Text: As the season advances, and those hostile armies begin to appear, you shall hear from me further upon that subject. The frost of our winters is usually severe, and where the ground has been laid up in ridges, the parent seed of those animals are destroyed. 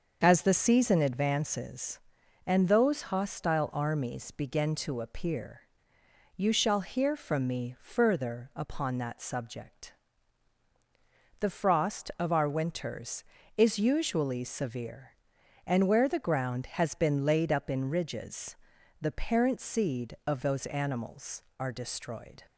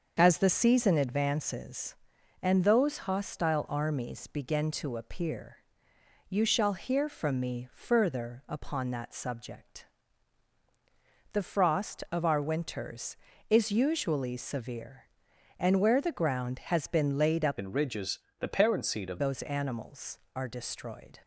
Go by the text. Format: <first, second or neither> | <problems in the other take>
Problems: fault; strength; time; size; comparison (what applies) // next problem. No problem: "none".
first | starts louder than the rest; until 1.2 s; 6.5 dB; also in the first // changes voice from "in" to "of"; from 17.5 to 19.1 s; 1.6 s long